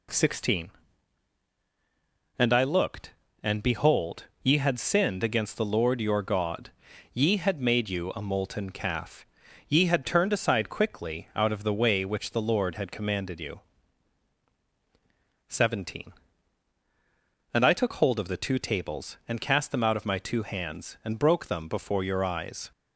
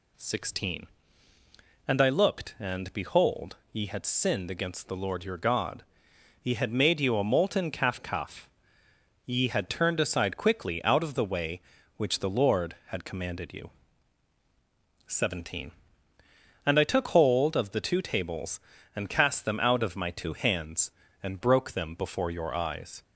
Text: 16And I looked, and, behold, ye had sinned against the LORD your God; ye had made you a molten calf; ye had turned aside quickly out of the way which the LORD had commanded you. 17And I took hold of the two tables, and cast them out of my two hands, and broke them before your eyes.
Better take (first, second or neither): first